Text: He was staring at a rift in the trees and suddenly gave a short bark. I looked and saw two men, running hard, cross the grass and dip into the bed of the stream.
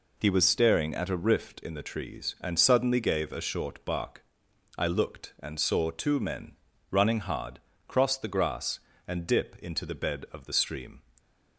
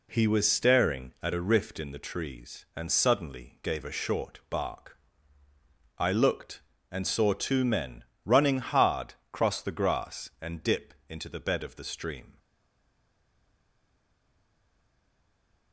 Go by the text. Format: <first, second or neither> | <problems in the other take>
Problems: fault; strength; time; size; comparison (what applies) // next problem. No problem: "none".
first | pauses between "dip" and "into"; slight; at 10.9 s; 0.16 s long // stays silent after the last word; strong; from 12.3 s on; 3.4 s long